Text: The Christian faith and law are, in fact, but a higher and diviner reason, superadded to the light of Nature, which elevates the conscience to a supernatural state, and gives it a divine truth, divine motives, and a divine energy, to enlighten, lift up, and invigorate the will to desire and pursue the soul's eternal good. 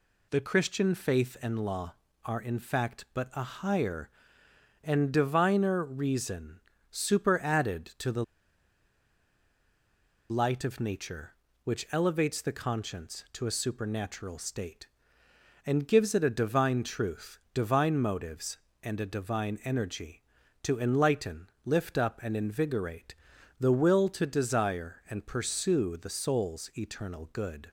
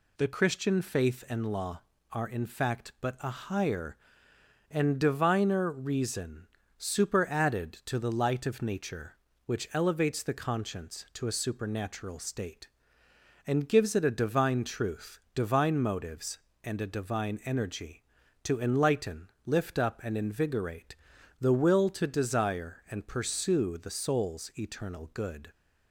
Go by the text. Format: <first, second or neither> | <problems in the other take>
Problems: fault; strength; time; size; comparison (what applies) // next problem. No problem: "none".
second | pauses between "the" and "light"; strong; at 8.2 s; 2.0 s long // pauses between "invigorate" and "the"; noticeable; at 23.1 s; 0.46 s long; noticeable in the second